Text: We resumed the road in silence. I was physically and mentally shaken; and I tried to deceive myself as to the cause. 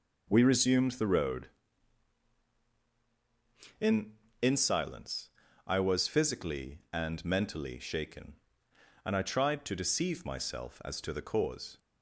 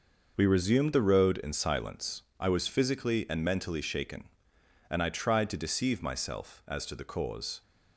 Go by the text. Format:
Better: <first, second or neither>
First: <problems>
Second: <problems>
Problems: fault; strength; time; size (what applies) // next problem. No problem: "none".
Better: second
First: says "in" twice; at 4.4 s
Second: none